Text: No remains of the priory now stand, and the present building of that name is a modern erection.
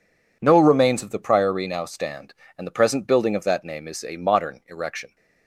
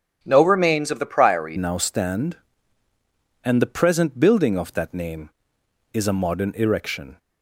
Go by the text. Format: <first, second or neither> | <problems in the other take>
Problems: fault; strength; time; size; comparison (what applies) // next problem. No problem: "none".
first | starts louder than the rest; strong; until 1.2 s; 8 dB // changes voice at "now"; from 1.5 s on; 5.6 s long